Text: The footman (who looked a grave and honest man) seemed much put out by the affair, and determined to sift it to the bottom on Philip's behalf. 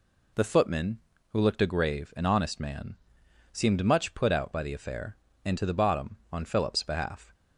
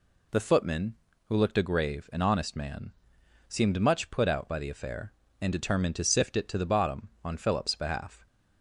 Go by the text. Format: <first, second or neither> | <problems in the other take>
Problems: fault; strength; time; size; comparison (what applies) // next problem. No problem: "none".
second | skips "determined to sift it"; at 5.5 s